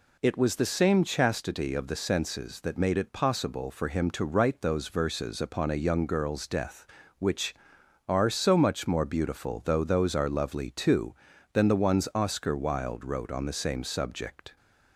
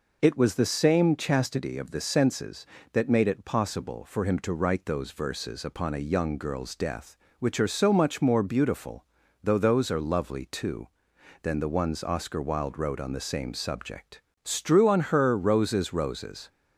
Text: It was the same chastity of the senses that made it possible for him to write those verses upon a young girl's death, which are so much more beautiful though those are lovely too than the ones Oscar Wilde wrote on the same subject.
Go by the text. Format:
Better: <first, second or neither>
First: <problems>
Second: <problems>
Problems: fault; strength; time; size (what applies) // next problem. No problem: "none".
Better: first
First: none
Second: pauses between "beautiful" and "though"; at 9.0 s; 0.38 s long // goes on to say "Strew on her roses roses"; strong; from 14.4 s on; 2.0 s long